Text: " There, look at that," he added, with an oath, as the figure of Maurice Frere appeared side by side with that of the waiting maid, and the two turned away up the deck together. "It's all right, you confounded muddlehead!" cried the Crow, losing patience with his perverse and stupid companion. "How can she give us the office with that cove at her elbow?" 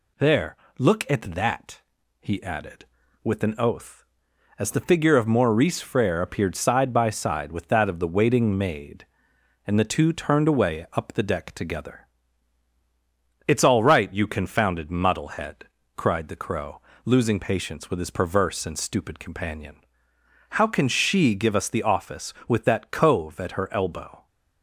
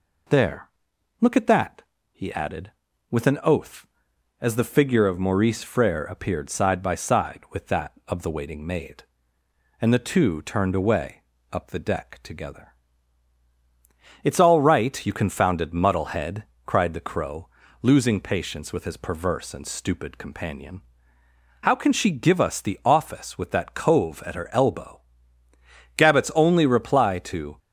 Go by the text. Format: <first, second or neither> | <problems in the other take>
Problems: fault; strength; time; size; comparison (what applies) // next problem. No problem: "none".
first | pauses between "away" and "up"; slight; at 11.2 s; 0.28 s long // goes on to say "Gabbett's only reply to"; from 25.9 s on; 1.6 s long